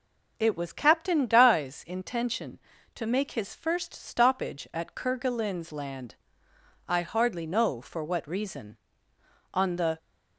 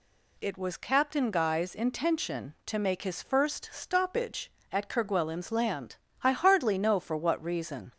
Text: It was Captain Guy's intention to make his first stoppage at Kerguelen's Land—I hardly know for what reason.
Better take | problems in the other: second | goes on to say "On the"; slight; from 9.5 s on; 0.44 s long

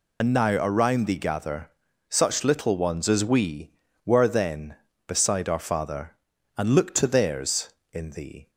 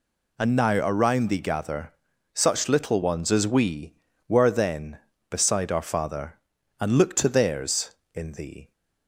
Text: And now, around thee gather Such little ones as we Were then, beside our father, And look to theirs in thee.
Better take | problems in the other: second | loses the start of "And"; at 0.2 s; 55 ms // pauses between "gather" and "Such"; at 1.7 s; 0.38 s long; also in the second

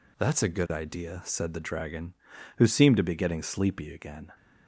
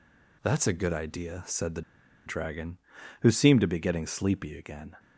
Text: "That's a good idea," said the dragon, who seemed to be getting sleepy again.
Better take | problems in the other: first | pauses between "the" and "dragon"; at 1.8 s; 0.45 s long

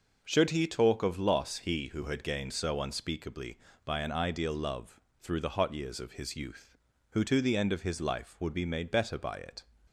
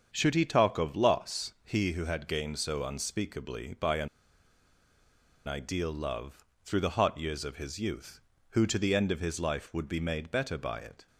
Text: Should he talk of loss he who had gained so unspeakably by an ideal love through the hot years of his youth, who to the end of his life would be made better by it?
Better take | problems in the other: first | starts louder than the rest; strong; until 1.1 s; 7 dB // pauses between "an" and "ideal"; strong; at 4.0 s; 1.4 s long // pauses between "love" and "through"; slight; at 6.4 s; 0.18 s long; slight in the first

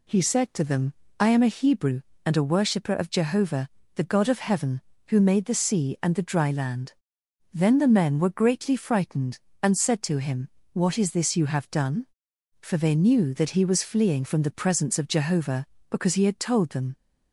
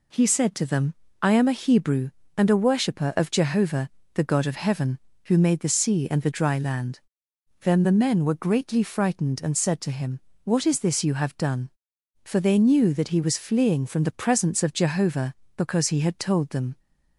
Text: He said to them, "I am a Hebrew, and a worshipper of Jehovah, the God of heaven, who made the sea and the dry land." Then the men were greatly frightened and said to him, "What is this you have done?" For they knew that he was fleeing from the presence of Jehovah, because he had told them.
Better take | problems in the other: neither | none

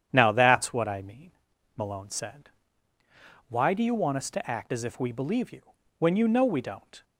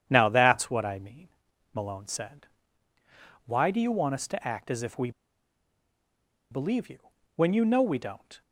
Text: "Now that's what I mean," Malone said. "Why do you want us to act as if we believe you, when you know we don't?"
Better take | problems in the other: first | starts louder than the rest; strong; until 1.0 s; 9 dB; strong in the first // pauses between "we" and "believe"; strong; at 5.1 s; 1.4 s long

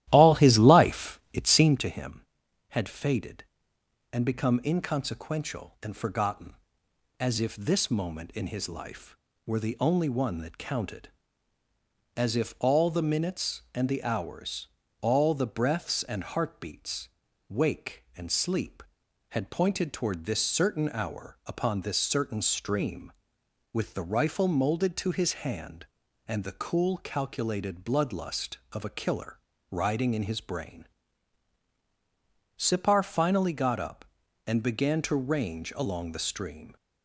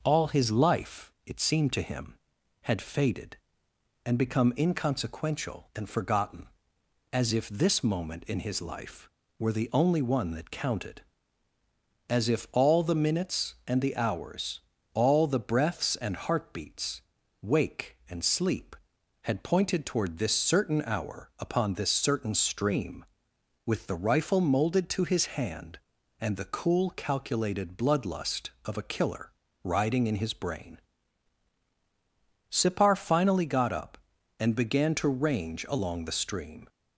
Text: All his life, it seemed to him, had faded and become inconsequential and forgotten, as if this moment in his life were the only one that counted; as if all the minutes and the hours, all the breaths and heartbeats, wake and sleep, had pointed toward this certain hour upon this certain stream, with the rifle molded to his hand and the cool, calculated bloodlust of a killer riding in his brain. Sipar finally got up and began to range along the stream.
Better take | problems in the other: second | starts louder than the rest; strong; until 1.8 s; 14 dB // pauses between "killer" and "riding"; slight; at 29.3 s; 0.36 s long; slight in the second

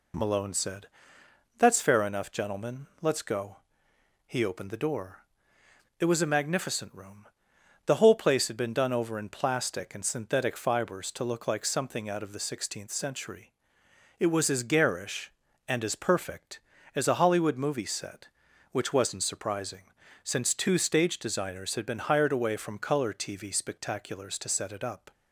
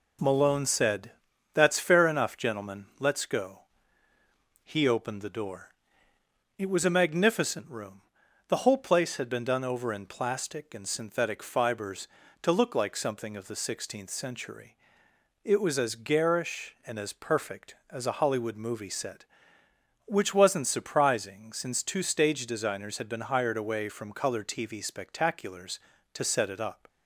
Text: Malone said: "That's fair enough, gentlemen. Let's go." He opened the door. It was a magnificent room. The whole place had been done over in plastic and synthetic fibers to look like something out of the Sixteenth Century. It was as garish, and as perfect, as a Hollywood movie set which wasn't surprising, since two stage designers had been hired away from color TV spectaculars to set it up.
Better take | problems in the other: first | skips "out"; at 13.3 s

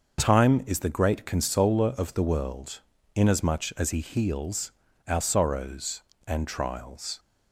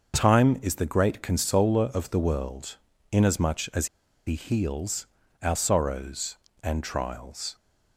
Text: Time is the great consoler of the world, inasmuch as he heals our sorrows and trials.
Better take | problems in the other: first | starts louder than the rest; until 1.1 s; 6 dB; also in the first // pauses between "as" and "he"; at 3.8 s; 0.39 s long // pauses between "heals" and "our"; slight; at 5.0 s; 0.34 s long; slight in the first

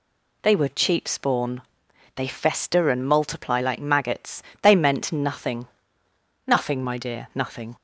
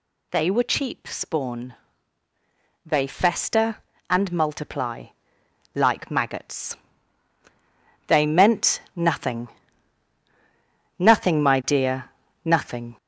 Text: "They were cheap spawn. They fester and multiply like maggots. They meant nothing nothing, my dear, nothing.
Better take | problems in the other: first | gets louder; noticeable; throughout; 4.5 dB // pauses between "multiply" and "like"; noticeable; at 5.0 s; 0.68 s long // pauses between "nothing" and "nothing"; strong; at 9.4 s; 1.4 s long; noticeable in the first

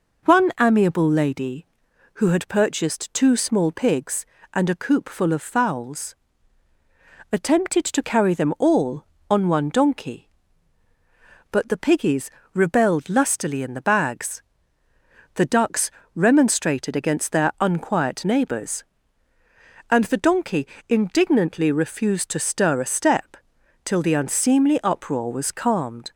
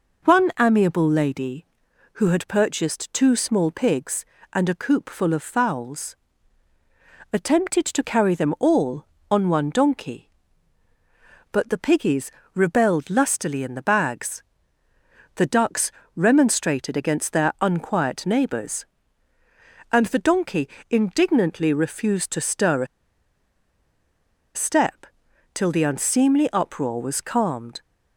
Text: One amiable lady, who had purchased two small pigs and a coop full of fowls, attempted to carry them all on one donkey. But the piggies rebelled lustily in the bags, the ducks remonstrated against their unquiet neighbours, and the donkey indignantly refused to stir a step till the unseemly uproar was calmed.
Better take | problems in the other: first | pauses between "piggies" and "rebelled"; slight; at 12.3 s; 0.24 s long; slight in the first // pauses between "ducks" and "remonstrated"; slight; at 15.9 s; 0.24 s long; slight in the first // pauses between "donkey" and "indignantly"; slight; at 20.6 s; 0.20 s long; slight in the first // pauses between "a" and "step"; strong; at 22.8 s; 1.6 s long // pauses between "step" and "till"; noticeable; at 25.0 s; 0.48 s long; noticeable in the first

